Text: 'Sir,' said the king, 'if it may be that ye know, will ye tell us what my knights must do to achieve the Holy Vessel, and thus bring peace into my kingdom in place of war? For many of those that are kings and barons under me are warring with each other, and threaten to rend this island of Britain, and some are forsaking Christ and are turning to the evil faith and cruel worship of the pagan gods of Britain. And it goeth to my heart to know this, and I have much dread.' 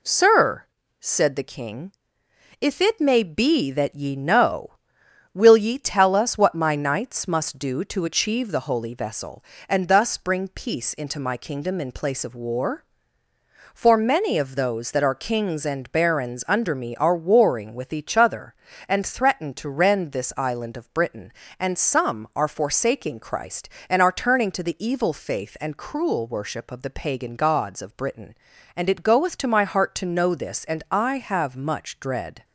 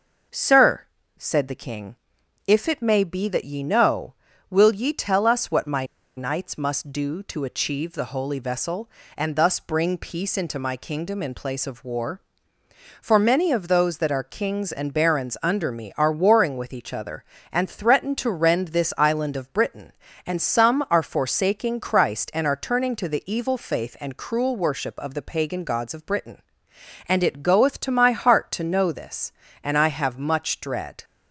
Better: first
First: none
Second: pauses between "my" and "knights"; slight; at 5.8 s; 0.31 s long

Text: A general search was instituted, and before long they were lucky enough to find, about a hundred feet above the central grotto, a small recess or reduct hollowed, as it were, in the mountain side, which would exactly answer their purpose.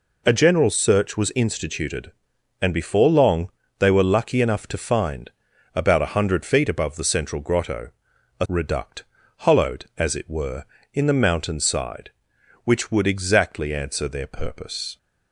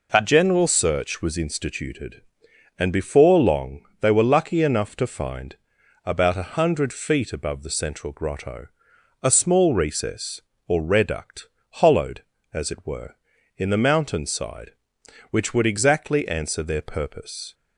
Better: second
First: pauses between "long" and "they"; slight; at 3.4 s; 0.30 s long // skips "small recess or"; at 8.4 s // pauses between "reduct" and "hollowed"; slight; at 9.0 s; 0.36 s long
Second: pauses between "long" and "they"; slight; at 3.8 s; 0.18 s long // pauses between "reduct" and "hollowed"; slight; at 11.4 s; 0.30 s long

